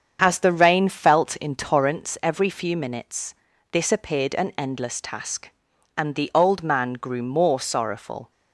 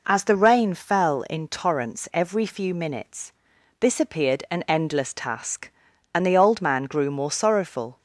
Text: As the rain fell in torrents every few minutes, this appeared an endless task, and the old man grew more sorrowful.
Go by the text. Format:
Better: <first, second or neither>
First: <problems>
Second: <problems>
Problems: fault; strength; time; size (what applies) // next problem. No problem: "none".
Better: second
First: starts louder than the rest; strong; until 1.2 s; 7.5 dB // says "felt" for "fell"; at 0.8 s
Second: none